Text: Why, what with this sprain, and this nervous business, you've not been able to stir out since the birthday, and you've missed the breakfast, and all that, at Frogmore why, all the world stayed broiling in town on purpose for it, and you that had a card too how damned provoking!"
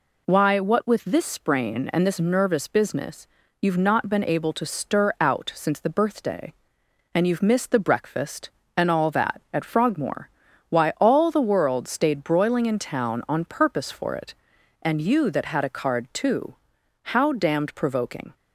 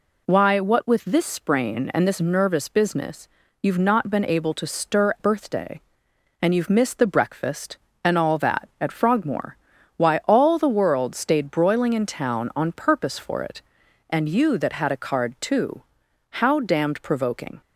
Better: first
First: pauses between "Frogmore" and "why"; at 10.2 s; 0.40 s long // pauses between "too" and "how"; noticeable; at 16.5 s; 0.58 s long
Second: skips "out since the"; at 5.1 s // pauses between "Frogmore" and "why"; at 9.5 s; 0.40 s long // pauses between "too" and "how"; noticeable; at 15.8 s; 0.58 s long

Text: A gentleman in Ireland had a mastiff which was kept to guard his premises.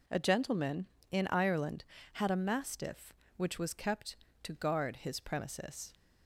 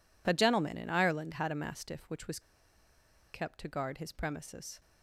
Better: first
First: none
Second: pauses between "was" and "kept"; noticeable; at 2.3 s; 0.92 s long

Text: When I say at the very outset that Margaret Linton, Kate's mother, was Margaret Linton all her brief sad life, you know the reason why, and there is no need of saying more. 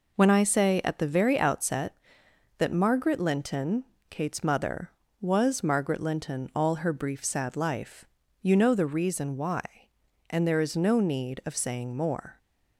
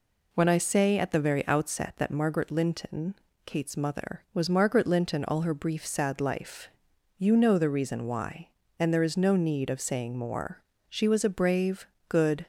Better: first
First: none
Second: goes on to say "She was a brave good"; from 10.8 s on; 1.5 s long

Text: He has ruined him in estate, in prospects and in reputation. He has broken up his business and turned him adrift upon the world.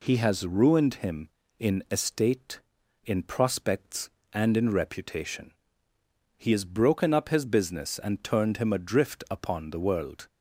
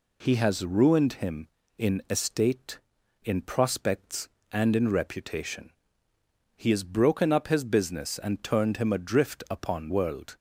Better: first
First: none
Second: skips "the"; at 9.8 s

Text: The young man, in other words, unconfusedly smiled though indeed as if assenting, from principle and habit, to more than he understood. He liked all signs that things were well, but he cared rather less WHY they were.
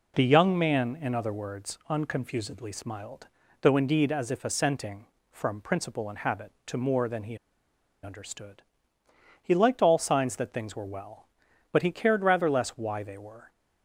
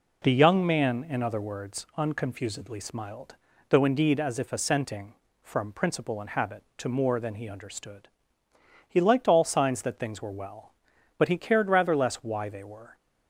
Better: second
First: pauses between "smiled" and "though"; slight; at 3.2 s; 0.34 s long // pauses between "he" and "understood"; noticeable; at 7.3 s; 0.68 s long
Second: pauses between "smiled" and "though"; slight; at 3.3 s; 0.34 s long

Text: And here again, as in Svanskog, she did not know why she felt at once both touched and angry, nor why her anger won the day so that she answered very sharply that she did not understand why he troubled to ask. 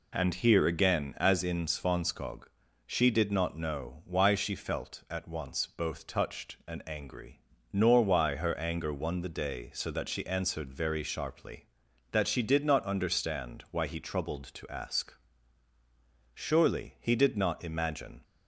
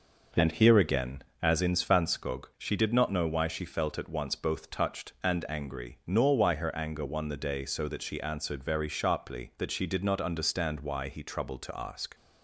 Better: second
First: goes on to say "Surely he did not imagine"; strong; from 16.3 s on; 1.8 s long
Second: none

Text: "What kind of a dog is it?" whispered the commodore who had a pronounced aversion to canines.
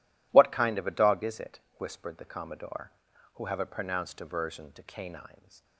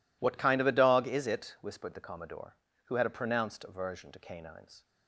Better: second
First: says "have" for "had"; at 3.4 s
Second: none

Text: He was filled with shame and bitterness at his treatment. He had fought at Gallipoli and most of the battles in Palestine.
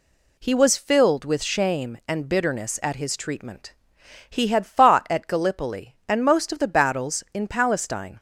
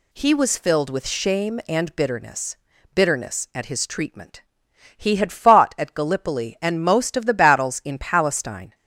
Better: first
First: none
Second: says "bitterness" twice; at 2.9 s

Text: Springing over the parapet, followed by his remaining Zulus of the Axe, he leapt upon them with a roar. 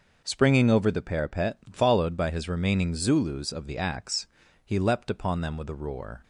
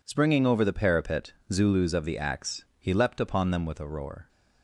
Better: first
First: none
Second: skips "followed by his remaining"; at 1.4 s

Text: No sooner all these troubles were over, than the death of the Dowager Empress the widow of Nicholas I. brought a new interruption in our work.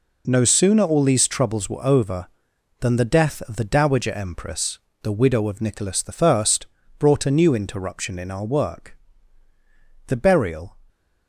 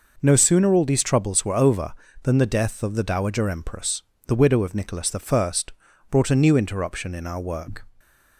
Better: second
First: pauses between "Empress" and "the"; slight; at 4.7 s; 0.24 s long // pauses between "Nicholas" and "I"; slight; at 6.0 s; 0.20 s long // pauses between "I" and "brought"; noticeable; at 6.4 s; 0.52 s long // goes on to say "The burial"; noticeable; from 10.0 s on; 0.70 s long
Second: pauses between "Empress" and "the"; slight; at 4.0 s; 0.24 s long // pauses between "I" and "brought"; noticeable; at 5.5 s; 0.60 s long

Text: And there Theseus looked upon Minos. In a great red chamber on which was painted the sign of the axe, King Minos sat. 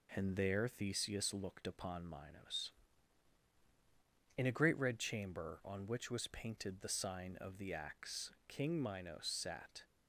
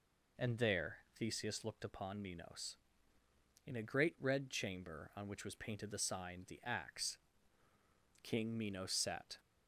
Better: first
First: none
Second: pauses between "there" and "Theseus"; slight; at 0.9 s; 0.18 s long // skips "of"; at 6.4 s

